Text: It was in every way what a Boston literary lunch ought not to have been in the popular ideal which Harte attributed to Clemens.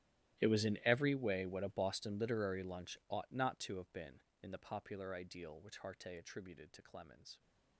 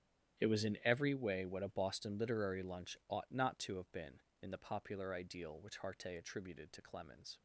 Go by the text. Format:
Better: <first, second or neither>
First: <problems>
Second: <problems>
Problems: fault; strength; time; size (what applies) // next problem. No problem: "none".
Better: second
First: gets quieter; strong; throughout; 22 dB // starts louder than the rest; strong; until 1.4 s; 14 dB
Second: starts louder than the rest; strong; until 1.4 s; 10.5 dB